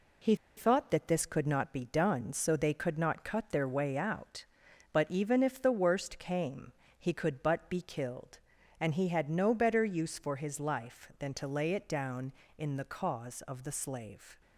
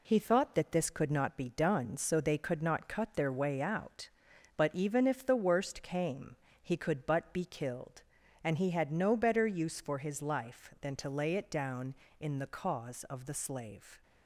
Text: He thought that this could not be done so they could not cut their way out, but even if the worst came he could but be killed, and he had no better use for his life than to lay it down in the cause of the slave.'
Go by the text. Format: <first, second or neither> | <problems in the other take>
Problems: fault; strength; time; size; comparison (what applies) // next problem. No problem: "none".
second | pauses between "He" and "thought"; slight; at 0.3 s; 0.20 s long // pauses between "came" and "he"; slight; at 6.7 s; 0.26 s long; slight in the second